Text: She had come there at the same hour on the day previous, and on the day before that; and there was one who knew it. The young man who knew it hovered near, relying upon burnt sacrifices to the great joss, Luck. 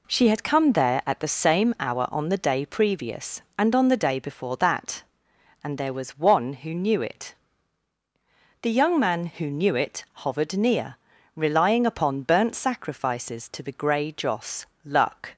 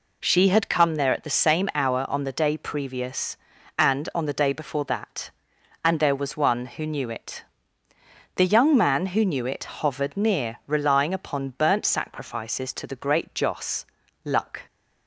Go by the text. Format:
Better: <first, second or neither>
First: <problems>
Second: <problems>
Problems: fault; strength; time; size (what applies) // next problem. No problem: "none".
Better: second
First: says "grey" for "great"; at 13.7 s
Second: none